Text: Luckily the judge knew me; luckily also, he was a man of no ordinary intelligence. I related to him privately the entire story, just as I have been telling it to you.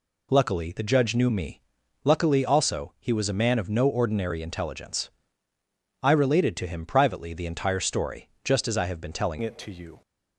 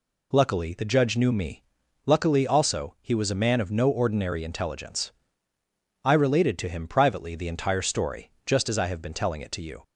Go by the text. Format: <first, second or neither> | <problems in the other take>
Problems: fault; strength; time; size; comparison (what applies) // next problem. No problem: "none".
second | changes voice at "it"; from 9.4 s on; 0.6 s long